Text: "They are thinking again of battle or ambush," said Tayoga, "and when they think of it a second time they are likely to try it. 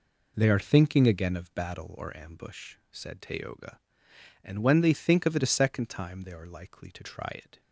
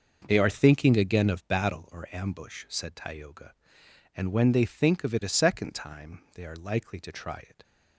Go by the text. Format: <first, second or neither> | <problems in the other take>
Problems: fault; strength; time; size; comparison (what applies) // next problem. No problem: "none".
neither | none